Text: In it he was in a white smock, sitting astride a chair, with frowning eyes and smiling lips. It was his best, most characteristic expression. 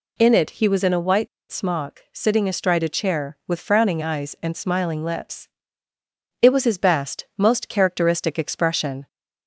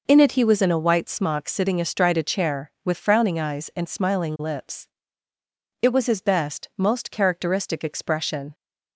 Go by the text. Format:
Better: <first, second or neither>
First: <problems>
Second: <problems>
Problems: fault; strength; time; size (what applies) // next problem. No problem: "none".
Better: second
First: pauses between "white" and "smock"; slight; at 1.2 s; 0.23 s long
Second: none